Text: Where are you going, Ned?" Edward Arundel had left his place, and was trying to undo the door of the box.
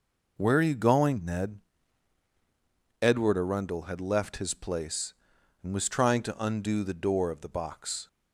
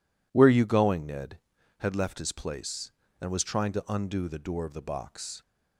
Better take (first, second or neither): first